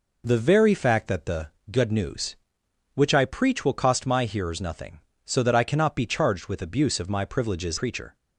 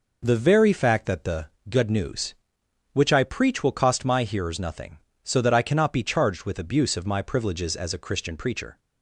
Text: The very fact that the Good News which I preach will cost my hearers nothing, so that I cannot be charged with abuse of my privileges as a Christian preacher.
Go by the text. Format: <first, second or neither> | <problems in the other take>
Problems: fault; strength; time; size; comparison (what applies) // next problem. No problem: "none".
second | pauses between "the" and "Good"; slight; at 1.4 s; 0.20 s long; slight in the second // skips "as a Christian"; at 7.7 s